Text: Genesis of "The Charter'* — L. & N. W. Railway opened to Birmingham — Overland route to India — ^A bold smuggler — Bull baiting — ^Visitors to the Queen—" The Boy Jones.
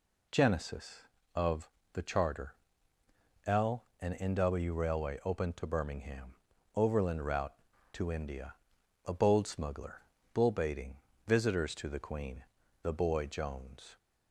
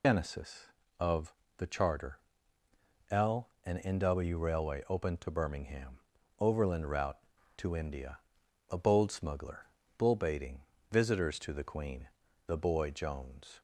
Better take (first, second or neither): first